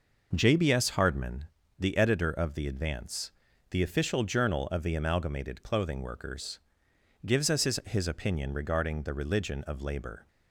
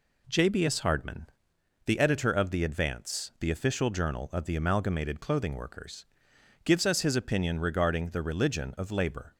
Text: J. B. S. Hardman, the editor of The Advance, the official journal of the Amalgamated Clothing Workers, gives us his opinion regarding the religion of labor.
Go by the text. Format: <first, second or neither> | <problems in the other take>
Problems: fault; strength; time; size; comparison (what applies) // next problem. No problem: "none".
second | says "his" twice; at 7.8 s